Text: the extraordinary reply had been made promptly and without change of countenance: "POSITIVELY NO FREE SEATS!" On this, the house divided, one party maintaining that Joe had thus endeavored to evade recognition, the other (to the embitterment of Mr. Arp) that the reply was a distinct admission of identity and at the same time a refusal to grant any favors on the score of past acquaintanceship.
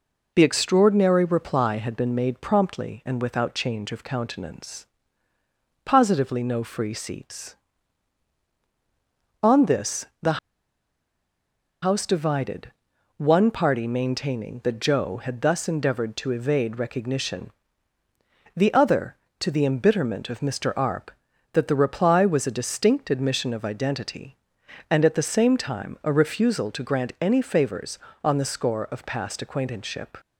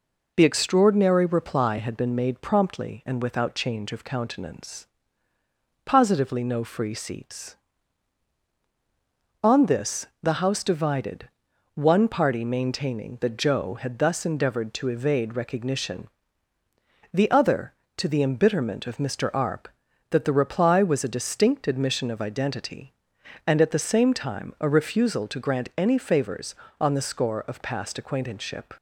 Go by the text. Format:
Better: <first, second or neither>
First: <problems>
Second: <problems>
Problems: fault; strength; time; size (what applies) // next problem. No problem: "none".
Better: second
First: pauses between "the" and "house"; strong; at 10.3 s; 1.4 s long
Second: none